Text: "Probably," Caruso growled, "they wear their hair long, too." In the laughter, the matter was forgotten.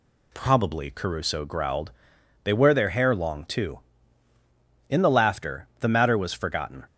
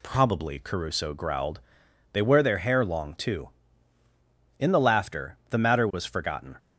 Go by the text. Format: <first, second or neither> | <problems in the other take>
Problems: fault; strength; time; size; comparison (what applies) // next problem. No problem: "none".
neither | none